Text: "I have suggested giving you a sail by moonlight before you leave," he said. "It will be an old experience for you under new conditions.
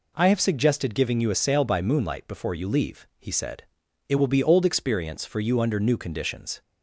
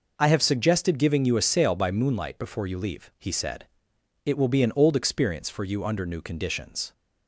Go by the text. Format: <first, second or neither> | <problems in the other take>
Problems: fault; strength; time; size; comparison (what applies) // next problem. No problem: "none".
second | skips "an"; at 4.4 s